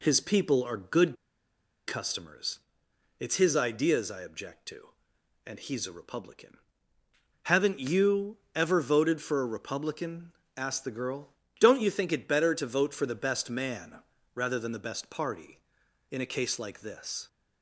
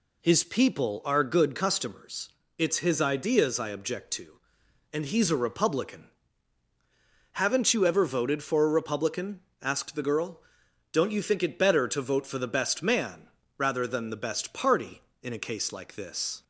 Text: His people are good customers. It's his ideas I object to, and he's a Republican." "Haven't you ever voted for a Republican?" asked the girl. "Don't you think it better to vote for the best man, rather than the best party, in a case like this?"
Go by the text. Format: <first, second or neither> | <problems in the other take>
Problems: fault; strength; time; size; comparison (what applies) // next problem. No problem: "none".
second | pauses between "good" and "customers"; noticeable; at 1.1 s; 0.73 s long // pauses between "you" and "ever"; slight; at 8.3 s; 0.18 s long